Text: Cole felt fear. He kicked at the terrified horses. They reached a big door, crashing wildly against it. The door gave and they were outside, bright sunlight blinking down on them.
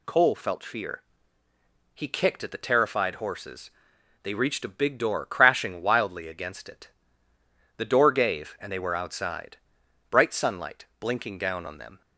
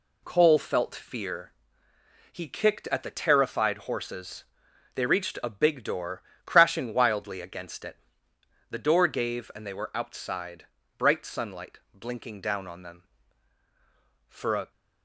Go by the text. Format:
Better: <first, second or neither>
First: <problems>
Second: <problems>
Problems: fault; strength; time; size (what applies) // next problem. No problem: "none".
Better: first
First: none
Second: goes on to say "For a"; slight; from 14.2 s on; 0.42 s long